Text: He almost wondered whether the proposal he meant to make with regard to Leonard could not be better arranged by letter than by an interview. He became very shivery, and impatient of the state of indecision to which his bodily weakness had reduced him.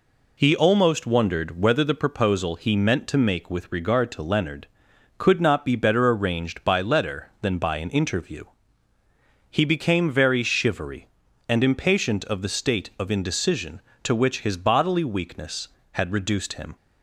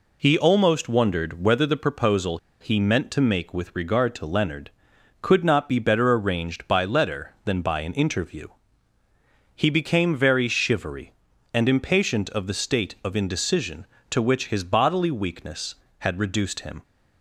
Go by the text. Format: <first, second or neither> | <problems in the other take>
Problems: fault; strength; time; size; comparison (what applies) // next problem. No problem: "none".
first | pauses between "proposal" and "he"; slight; at 2.3 s; 0.23 s long